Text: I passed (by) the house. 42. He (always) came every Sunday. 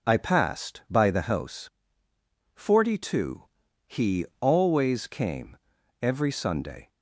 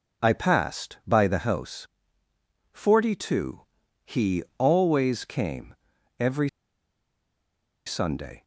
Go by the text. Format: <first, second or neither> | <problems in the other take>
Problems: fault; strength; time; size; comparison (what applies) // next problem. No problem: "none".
first | pauses between "came" and "every"; at 5.7 s; 0.44 s long; also in the first // pauses between "every" and "Sunday"; strong; at 6.4 s; 1.3 s long